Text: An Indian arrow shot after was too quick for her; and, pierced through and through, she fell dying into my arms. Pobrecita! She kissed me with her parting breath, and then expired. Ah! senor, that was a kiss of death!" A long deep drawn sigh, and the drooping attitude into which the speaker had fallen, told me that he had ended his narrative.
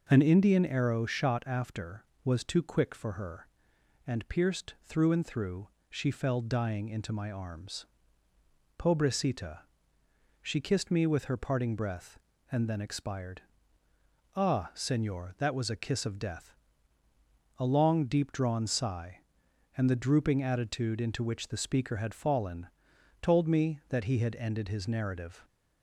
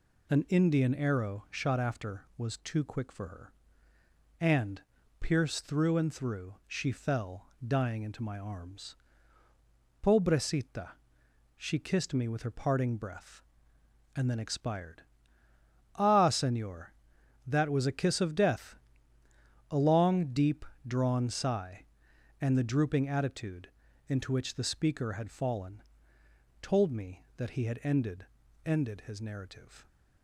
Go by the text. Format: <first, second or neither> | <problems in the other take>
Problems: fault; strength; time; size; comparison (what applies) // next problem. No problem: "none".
first | pauses between "fell" and "dying"; slight; at 7.4 s; 0.18 s long // pauses between "deep" and "drawn"; slight; at 20.6 s; 0.24 s long // pauses between "attitude" and "into"; at 23.6 s; 0.40 s long // says "ended" twice; at 28.6 s